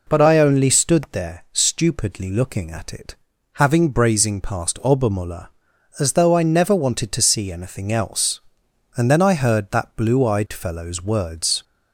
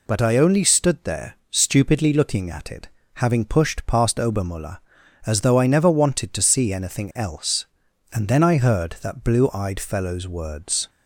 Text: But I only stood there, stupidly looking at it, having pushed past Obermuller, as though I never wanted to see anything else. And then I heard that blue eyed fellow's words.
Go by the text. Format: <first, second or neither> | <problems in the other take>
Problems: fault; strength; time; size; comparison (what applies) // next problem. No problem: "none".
second | says "brazing" for "pushed"; at 3.9 s